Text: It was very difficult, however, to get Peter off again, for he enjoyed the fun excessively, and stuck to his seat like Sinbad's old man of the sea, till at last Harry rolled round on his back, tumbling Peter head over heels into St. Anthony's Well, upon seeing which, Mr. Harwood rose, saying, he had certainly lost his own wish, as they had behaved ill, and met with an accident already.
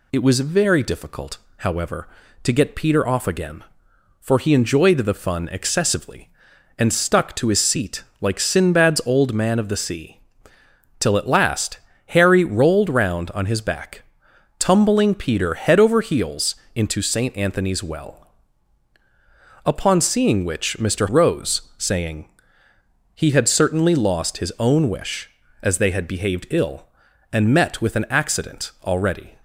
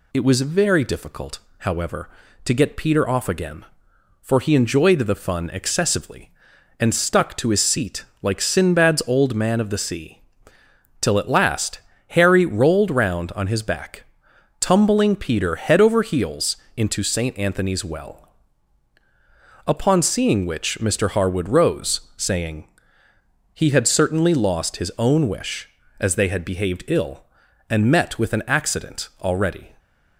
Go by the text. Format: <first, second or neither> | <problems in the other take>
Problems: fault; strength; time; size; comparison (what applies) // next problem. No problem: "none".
second | pauses between "seat" and "like"; slight; at 8.0 s; 0.16 s long; slight in the second // pauses between "last" and "Harry"; slight; at 11.7 s; 0.32 s long; slight in the second // pauses between "heels" and "into"; slight; at 16.5 s; 0.20 s long; slight in the second // skips "Harwood"; at 21.0 s